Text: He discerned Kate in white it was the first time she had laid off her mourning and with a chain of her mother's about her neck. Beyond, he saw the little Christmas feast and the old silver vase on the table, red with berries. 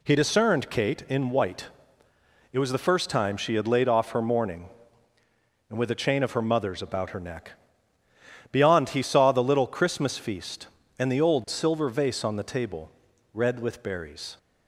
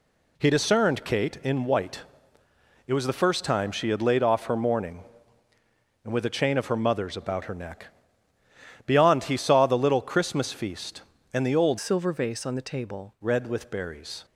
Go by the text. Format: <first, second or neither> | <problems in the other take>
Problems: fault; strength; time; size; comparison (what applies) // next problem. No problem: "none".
first | pauses between "white" and "it"; noticeable; at 2.0 s; 0.86 s long; noticeable in the first // changes voice from "silver" to "table"; from 11.7 to 13.1 s; 1.4 s long